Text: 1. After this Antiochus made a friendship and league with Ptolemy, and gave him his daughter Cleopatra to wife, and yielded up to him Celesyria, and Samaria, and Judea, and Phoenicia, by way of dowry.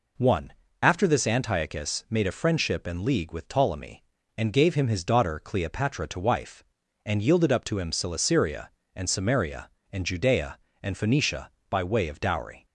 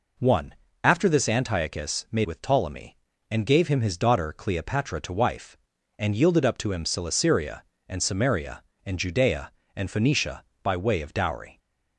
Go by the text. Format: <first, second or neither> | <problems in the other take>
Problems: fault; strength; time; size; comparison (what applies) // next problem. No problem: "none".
first | skips "a friendship and league"; at 2.2 s